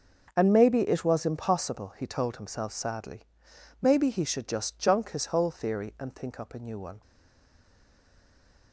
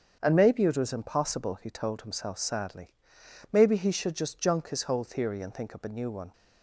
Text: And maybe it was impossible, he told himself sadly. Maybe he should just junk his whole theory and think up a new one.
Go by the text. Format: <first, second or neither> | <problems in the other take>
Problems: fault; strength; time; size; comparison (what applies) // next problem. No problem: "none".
second | starts louder than the rest; until 1.3 s; 6.5 dB; strong in the second // stays silent after the last word; noticeable; from 7.0 s on; 1.7 s long